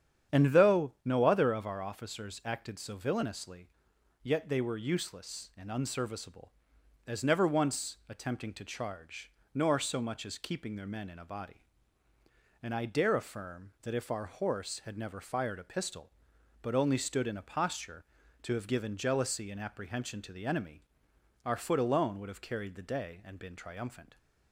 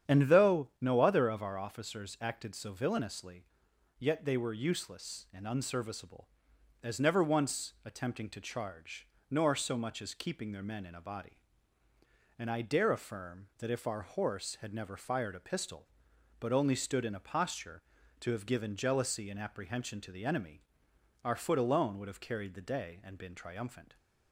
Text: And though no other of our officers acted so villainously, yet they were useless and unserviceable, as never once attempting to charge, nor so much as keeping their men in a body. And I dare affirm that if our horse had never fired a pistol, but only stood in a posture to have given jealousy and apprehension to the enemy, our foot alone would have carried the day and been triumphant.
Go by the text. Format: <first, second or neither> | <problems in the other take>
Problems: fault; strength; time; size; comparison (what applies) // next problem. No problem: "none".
neither | starts louder than the rest; strong; the same in both